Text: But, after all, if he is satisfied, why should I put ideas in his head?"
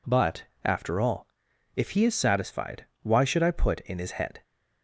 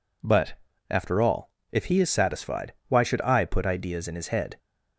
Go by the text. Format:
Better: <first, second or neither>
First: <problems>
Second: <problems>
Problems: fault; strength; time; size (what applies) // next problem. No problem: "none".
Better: second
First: skips "ideas"; at 3.7 s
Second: none